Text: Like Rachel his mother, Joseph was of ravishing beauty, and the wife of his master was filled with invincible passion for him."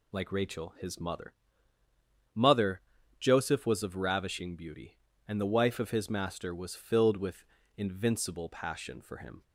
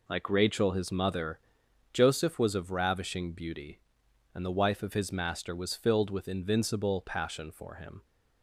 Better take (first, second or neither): second